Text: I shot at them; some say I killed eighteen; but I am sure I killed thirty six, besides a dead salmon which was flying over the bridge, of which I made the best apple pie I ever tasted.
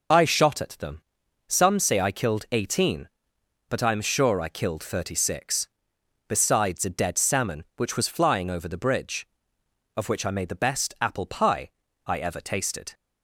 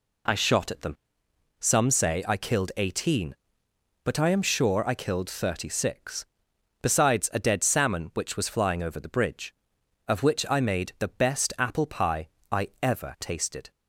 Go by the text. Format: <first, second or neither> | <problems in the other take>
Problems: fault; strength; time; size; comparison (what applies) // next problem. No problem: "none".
second | loses the start of "I"; at 0.1 s; 25 ms // pauses between "pie" and "I"; slight; at 11.6 s; 0.36 s long; slight in the second